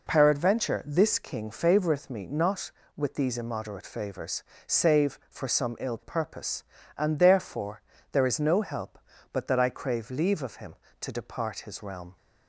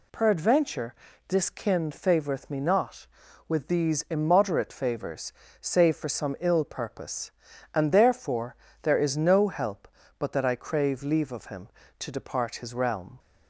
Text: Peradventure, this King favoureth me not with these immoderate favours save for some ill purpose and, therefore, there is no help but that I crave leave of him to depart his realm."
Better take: first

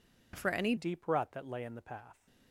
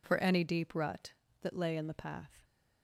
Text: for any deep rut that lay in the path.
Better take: second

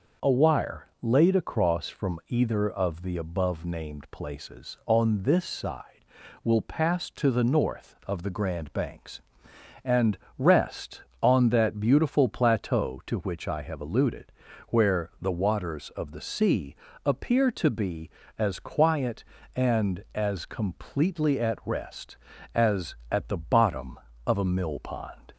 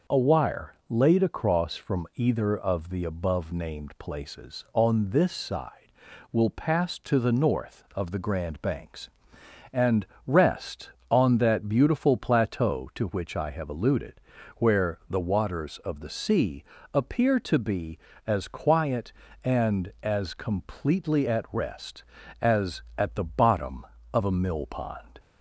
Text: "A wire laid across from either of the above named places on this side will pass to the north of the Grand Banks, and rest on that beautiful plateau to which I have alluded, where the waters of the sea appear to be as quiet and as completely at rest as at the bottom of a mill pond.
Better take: neither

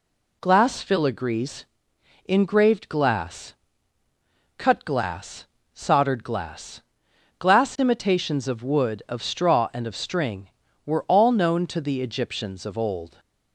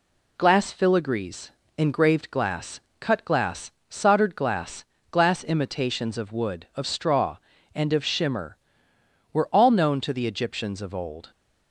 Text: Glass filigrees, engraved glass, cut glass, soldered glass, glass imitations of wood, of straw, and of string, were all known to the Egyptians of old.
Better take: first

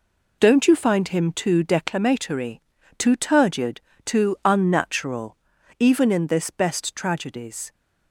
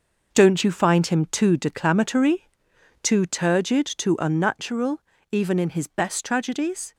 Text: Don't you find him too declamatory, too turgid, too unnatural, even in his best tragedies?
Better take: second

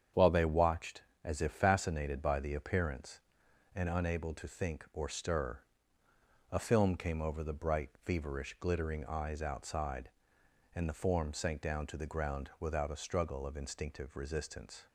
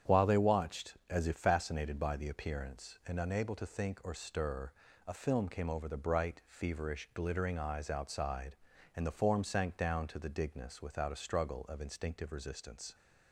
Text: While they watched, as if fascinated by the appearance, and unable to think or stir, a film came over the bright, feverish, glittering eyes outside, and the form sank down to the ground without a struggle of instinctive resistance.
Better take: first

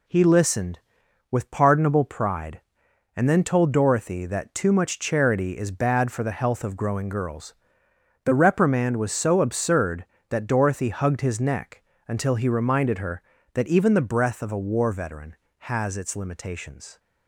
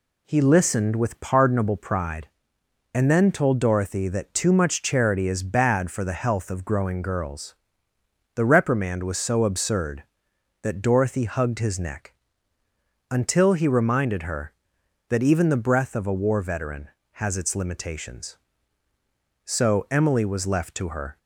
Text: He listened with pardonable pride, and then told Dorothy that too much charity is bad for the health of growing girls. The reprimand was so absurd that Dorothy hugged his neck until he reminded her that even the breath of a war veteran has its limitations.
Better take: first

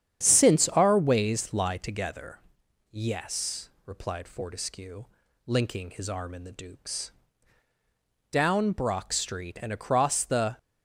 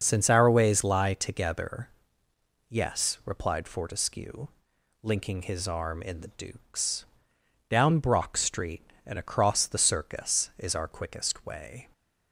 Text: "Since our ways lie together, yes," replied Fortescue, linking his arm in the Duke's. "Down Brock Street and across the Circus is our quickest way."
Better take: second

